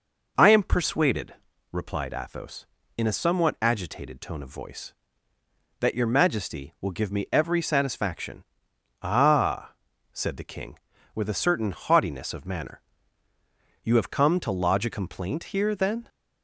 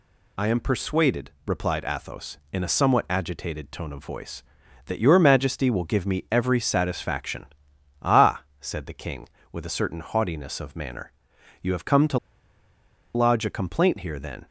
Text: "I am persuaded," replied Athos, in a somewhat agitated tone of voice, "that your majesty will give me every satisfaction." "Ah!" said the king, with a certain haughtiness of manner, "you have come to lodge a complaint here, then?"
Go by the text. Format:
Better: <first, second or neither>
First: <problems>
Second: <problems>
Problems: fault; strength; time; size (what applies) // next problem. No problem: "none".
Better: first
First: none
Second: pauses between "to" and "lodge"; noticeable; at 12.1 s; 0.96 s long